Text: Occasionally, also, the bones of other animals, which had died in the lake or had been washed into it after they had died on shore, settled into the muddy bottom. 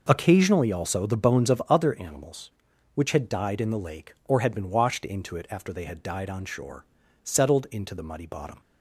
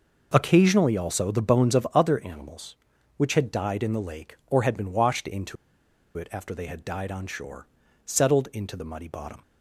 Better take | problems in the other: first | pauses between "into" and "it"; noticeable; at 5.5 s; 0.61 s long

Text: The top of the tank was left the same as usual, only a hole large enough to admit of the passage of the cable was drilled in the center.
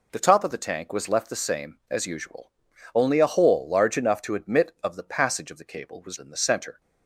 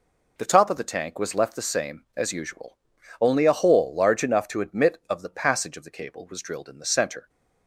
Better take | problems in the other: second | skips "drilled"; at 6.1 s

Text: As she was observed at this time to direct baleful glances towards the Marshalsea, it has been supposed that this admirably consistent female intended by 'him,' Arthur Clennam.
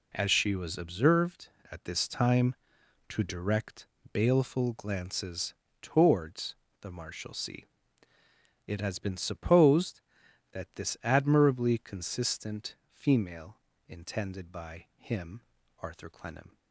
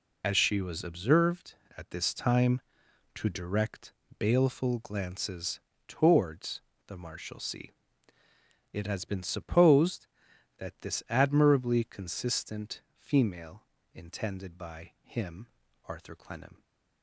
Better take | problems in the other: first | loses the start of "As"; at 0.2 s; 60 ms // pauses between "direct" and "baleful"; slight; at 3.9 s; 0.26 s long; slight in the first // pauses between "glances" and "towards"; slight; at 5.6 s; 0.26 s long; slight in the first // pauses between "towards" and "the"; slight; at 6.6 s; 0.26 s long; slight in the first // pauses between "consistent" and "female"; slight; at 12.8 s; 0.16 s long; slight in the first // pauses between "female" and "intended"; slight; at 13.6 s; 0.32 s long; slight in the first

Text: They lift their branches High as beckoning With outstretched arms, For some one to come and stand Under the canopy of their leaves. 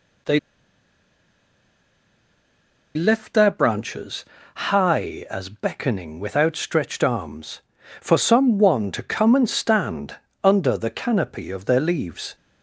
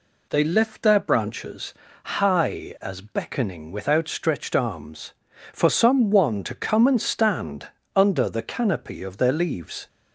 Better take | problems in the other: second | pauses between "They" and "lift"; strong; at 0.3 s; 2.5 s long // pauses between "branches" and "High"; slight; at 4.2 s; 0.30 s long; slight in the second // pauses between "stand" and "Under"; slight; at 10.1 s; 0.28 s long; slight in the second

